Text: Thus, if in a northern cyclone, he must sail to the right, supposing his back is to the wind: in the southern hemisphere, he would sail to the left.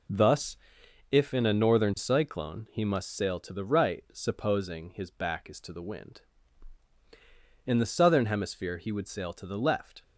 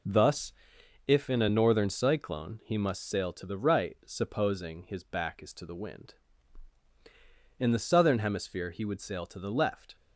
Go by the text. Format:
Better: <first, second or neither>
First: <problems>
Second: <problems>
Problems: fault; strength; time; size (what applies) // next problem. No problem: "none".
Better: neither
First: none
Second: none